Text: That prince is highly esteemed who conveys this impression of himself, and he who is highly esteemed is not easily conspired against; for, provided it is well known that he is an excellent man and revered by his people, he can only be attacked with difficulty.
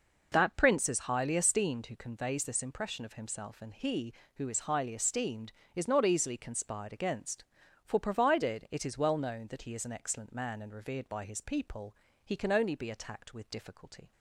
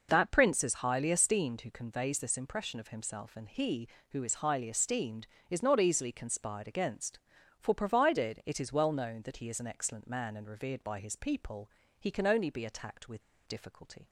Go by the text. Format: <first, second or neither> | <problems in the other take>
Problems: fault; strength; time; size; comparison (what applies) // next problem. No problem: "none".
first | pauses between "with" and "difficulty"; slight; at 13.2 s; 0.25 s long